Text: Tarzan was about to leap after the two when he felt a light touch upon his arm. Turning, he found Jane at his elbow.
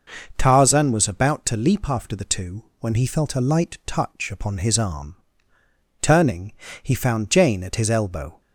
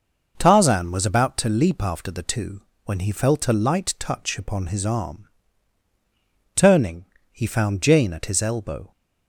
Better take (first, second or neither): neither